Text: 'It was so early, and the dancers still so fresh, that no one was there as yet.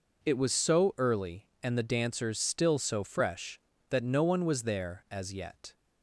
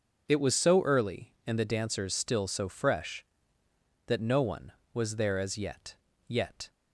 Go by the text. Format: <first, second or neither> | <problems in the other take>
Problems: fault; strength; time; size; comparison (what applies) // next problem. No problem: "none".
first | says "yet" twice; at 6.2 s